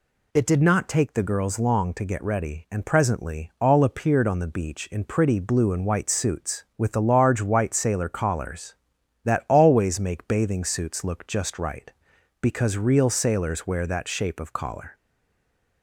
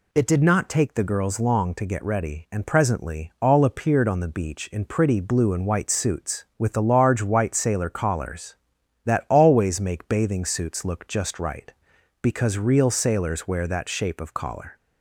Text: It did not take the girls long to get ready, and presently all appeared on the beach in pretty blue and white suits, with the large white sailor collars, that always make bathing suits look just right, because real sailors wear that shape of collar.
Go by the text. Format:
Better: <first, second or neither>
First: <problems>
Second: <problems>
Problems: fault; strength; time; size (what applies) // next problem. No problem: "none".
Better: second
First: stays silent after the last word; slight; from 14.9 s on; 0.9 s long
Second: none